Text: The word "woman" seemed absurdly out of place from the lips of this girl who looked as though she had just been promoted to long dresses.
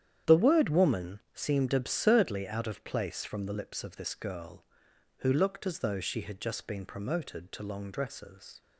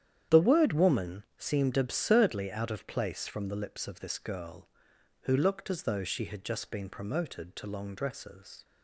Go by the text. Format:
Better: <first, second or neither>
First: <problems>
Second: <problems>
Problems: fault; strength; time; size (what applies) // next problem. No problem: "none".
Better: neither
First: starts louder than the rest; strong; until 1.4 s; 9.5 dB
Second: starts louder than the rest; strong; until 1.4 s; 9.5 dB